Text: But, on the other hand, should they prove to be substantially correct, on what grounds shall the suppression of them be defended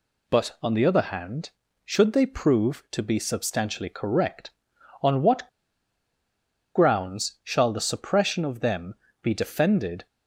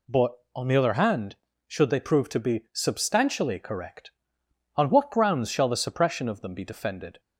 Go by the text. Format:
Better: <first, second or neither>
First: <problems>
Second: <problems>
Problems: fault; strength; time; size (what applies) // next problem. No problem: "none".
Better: second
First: pauses between "what" and "grounds"; strong; at 5.4 s; 1.2 s long // pauses between "them" and "be"; slight; at 8.9 s; 0.28 s long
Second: none